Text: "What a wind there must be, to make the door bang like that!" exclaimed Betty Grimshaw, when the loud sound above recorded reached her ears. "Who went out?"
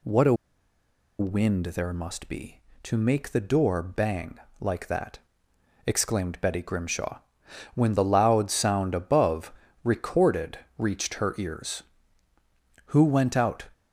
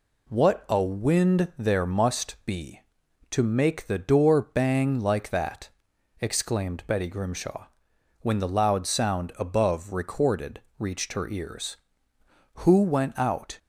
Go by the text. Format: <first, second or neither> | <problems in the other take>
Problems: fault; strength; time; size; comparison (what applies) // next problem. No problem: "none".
second | pauses between "a" and "wind"; noticeable; at 0.3 s; 0.85 s long // pauses between "bang" and "like"; slight; at 4.3 s; 0.22 s long // pauses between "above" and "recorded"; slight; at 9.5 s; 0.32 s long // pauses between "recorded" and "reached"; slight; at 10.5 s; 0.20 s long; slight in the second